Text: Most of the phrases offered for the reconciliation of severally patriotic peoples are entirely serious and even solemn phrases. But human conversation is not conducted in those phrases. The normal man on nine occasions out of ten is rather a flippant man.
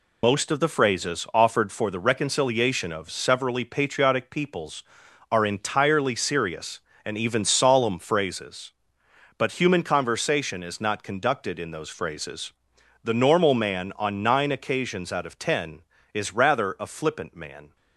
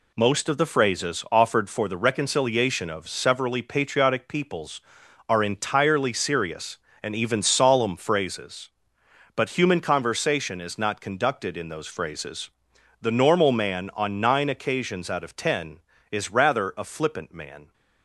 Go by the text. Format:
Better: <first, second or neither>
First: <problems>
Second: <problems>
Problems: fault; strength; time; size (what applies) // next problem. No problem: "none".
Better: second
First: loses the start of "Most"; at 0.2 s; 65 ms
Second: none